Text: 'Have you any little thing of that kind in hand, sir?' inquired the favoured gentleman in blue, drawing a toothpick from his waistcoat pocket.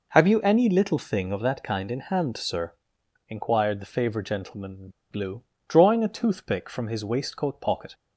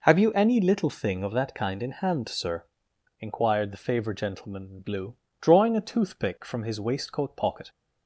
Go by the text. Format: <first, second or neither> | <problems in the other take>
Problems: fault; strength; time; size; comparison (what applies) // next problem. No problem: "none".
second | pauses between "in" and "blue"; slight; at 4.8 s; 0.21 s long